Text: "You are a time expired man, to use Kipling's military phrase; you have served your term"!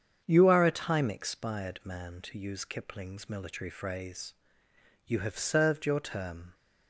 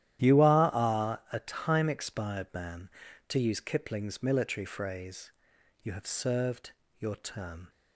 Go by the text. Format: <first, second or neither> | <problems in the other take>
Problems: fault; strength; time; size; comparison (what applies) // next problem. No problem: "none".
first | starts louder than the rest; strong; until 1.3 s; 12 dB; strong in the first // says "are" twice; at 0.7 s // pauses between "served" and "your"; slight; at 6.7 s; 0.26 s long